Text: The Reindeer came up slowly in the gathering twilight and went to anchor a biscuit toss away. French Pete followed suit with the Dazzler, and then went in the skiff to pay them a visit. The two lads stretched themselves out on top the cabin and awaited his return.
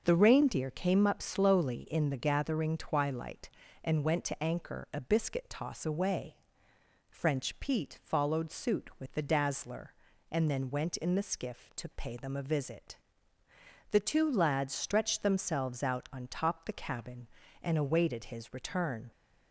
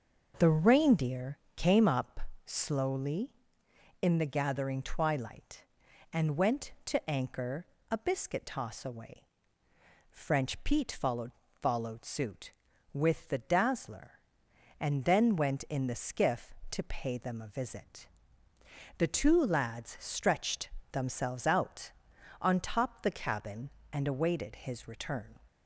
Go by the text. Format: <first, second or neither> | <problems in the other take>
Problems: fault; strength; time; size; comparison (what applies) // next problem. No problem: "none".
first | starts louder than the rest; noticeable; until 1.3 s; 6 dB; also in the first // pauses between "Reindeer" and "came"; slight; at 1.3 s; 0.18 s long // pauses between "up" and "slowly"; slight; at 2.1 s; 0.26 s long // pauses between "anchor" and "a"; slight; at 7.6 s; 0.22 s long // says "followed" twice; at 11.6 s // pauses between "stretched" and "themselves"; slight; at 20.6 s; 0.22 s long